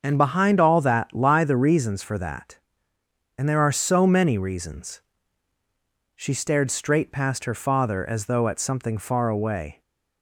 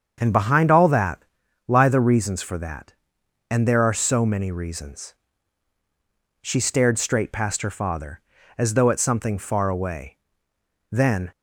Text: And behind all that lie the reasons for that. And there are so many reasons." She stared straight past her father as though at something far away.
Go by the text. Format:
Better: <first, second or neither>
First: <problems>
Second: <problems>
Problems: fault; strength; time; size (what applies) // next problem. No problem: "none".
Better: first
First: starts louder than the rest; until 1.0 s; 6.5 dB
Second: starts louder than the rest; strong; until 1.2 s; 7 dB // pauses between "that" and "lie"; at 1.2 s; 0.44 s long // goes on to say "Then"; slight; from 10.9 s on; 0.40 s long